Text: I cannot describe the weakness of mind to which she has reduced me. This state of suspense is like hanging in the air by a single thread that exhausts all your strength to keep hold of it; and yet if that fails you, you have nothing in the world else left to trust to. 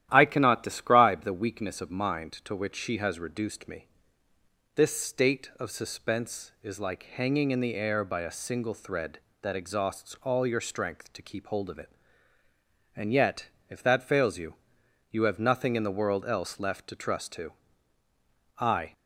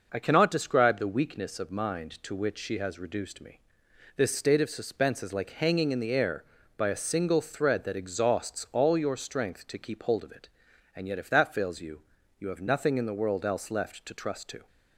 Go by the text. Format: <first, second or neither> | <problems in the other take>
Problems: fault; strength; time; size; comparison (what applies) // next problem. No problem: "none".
second | starts louder than the rest; strong; until 1.1 s; 12 dB // pauses between "yet" and "if"; slight; at 13.4 s; 0.20 s long // goes on to say "I"; slight; from 18.5 s on; 0.36 s long